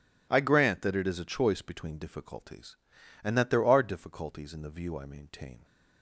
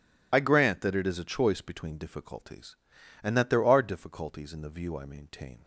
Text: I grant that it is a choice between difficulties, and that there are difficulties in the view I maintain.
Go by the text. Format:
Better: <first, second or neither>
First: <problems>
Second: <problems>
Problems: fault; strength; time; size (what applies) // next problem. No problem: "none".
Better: first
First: none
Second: loses the start of "I"; at 0.3 s; 30 ms